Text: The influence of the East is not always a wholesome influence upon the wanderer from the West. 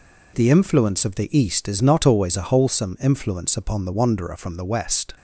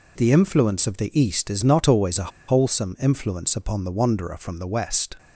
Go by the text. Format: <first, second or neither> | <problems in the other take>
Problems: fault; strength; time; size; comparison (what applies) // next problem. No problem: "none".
first | pauses between "a" and "wholesome"; slight; at 2.3 s; 0.17 s long